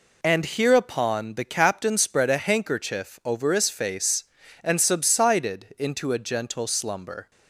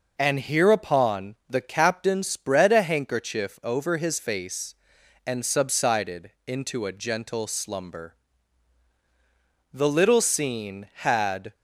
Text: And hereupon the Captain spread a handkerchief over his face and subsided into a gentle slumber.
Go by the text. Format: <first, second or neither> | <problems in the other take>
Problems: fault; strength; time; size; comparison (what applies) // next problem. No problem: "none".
first | pauses between "subsided" and "into"; slight; at 6.2 s; 0.16 s long // goes on to say "The little scene had"; strong; from 9.7 s on; 1.8 s long